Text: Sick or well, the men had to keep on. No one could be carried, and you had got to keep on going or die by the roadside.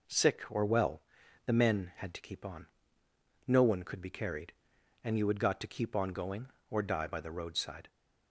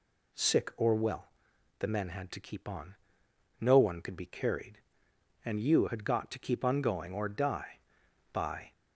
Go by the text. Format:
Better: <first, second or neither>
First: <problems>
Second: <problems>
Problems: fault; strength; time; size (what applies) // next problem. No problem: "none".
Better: first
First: none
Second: stops before "the roadside"; at 8.7 s